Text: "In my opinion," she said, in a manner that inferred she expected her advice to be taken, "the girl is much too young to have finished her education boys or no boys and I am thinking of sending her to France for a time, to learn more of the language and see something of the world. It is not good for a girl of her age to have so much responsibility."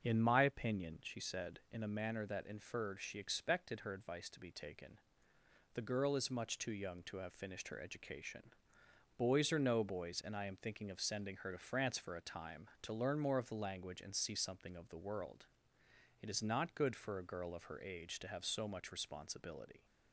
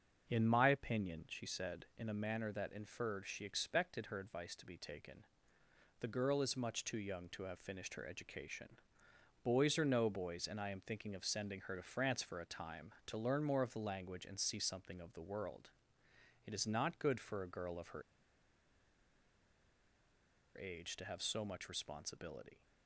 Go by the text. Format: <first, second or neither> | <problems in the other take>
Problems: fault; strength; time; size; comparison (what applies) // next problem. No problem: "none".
first | starts louder than the rest; until 1.3 s; 6.5 dB; also in the first // pauses between "education" and "boys"; noticeable; at 8.7 s; 0.68 s long; noticeable in the first // pauses between "her" and "age"; strong; at 18.0 s; 2.5 s long